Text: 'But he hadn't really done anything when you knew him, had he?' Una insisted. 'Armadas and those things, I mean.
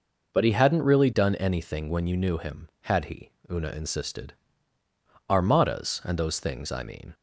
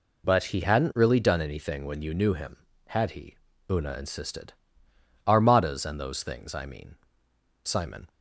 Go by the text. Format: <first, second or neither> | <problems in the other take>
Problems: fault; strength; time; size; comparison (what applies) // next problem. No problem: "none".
first | goes on to say "Simon"; slight; from 7.6 s on; 0.44 s long